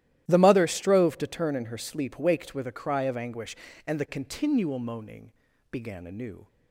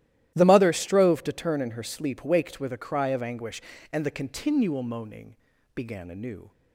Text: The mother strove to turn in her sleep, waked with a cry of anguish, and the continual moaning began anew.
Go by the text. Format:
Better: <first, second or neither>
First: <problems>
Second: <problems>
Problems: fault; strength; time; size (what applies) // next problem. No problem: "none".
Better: neither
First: starts louder than the rest; strong; until 1.2 s; 13.5 dB // pauses between "moaning" and "began"; at 5.3 s; 0.40 s long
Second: starts louder than the rest; strong; until 1.3 s; 13.5 dB // pauses between "moaning" and "began"; at 5.3 s; 0.40 s long